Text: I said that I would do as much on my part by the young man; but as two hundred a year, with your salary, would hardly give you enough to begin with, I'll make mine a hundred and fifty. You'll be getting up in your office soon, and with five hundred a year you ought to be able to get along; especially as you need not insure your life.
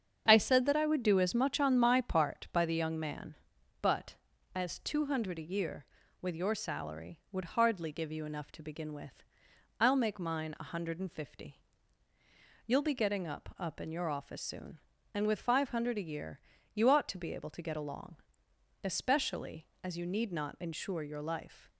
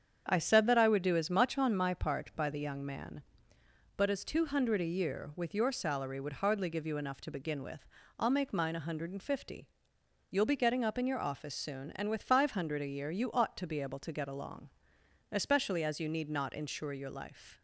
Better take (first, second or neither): second